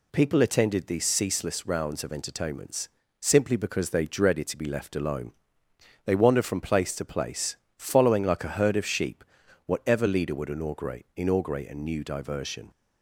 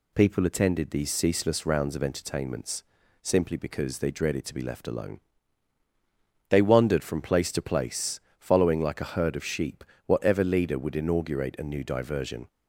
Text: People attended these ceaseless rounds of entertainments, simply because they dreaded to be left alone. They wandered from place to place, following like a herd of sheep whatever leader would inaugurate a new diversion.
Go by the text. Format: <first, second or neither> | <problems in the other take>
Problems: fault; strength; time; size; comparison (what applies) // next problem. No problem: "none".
second | pauses between "sheep" and "whatever"; at 9.2 s; 0.44 s long; slight in the second // says "inaugurate" twice; at 11.1 s